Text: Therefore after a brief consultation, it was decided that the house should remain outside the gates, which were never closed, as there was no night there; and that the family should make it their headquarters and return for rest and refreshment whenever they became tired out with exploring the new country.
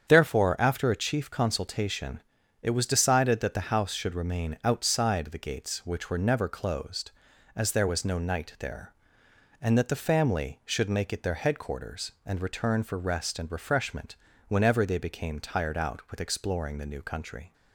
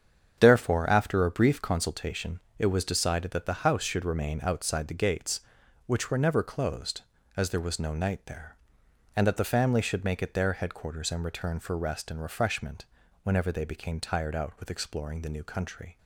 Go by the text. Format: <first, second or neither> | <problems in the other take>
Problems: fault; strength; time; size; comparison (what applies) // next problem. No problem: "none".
second | starts louder than the rest; strong; until 1.1 s; 8 dB; strong in the second // says "chief" for "brief"; at 0.9 s // pauses between "refreshment" and "whenever"; slight; at 14.1 s; 0.34 s long; also in the second